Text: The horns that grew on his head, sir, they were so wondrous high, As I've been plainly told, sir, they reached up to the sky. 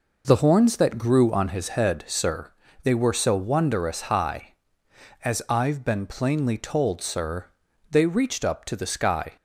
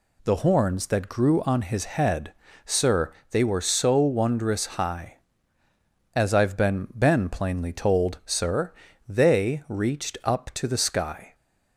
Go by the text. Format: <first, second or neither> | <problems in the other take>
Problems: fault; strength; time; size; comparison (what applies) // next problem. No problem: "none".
first | says "been" twice; at 6.9 s